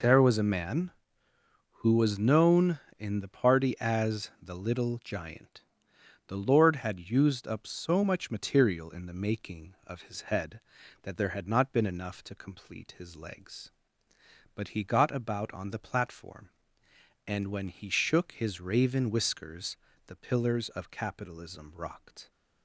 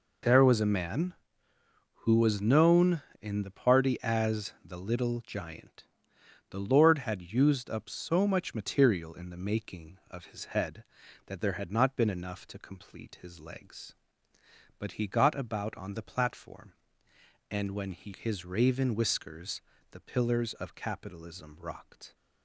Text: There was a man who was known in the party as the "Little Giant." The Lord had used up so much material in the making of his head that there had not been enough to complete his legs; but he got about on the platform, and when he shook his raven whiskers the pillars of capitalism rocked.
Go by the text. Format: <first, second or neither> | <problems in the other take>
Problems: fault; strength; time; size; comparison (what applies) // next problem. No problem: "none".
first | skips "shook"; at 18.1 s // pauses between "whiskers" and "the"; slight; at 19.6 s; 0.30 s long; slight in the first